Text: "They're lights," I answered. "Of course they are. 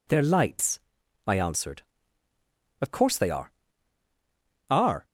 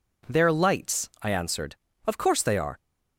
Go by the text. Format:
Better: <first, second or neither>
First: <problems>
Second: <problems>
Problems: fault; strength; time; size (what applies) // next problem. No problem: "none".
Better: second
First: says "are" twice; at 4.6 s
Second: none